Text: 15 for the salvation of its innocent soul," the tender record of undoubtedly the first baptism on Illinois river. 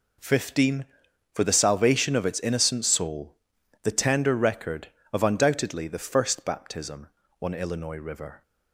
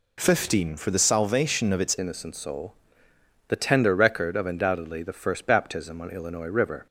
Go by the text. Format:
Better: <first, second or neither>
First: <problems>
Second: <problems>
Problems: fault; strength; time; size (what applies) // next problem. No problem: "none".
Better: first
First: none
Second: changes voice at "innocent"; from 1.9 s on; 4.9 s long